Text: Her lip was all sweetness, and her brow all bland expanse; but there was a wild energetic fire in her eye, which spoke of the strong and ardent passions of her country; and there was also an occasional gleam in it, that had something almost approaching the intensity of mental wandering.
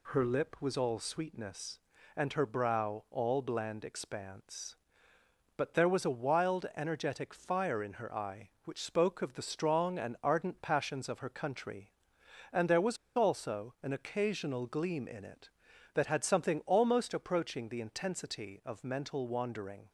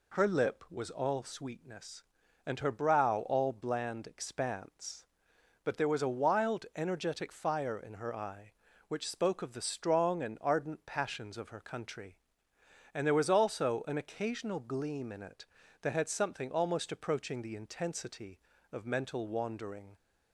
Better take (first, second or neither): second